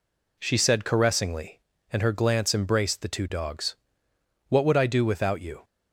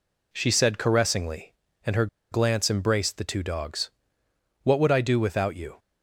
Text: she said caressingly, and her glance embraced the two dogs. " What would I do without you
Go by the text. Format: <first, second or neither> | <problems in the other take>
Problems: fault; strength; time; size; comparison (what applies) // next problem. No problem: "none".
first | pauses between "her" and "glance"; slight; at 2.0 s; 0.25 s long